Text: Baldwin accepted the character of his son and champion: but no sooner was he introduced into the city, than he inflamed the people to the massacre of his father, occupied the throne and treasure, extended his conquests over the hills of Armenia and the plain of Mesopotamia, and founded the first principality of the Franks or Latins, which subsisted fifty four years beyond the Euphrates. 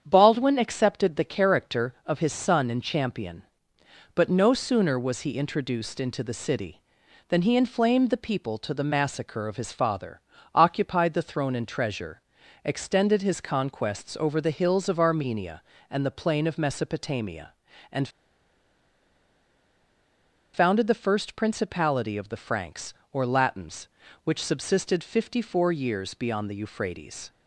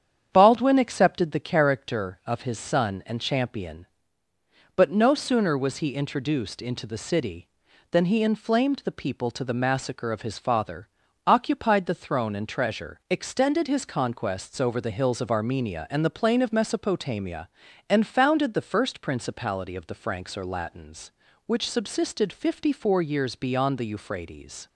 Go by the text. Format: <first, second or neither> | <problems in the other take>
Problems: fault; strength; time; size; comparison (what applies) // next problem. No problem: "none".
second | starts louder than the rest; strong; until 1.0 s; 8 dB; strong in the second // pauses between "and" and "founded"; strong; at 18.0 s; 2.4 s long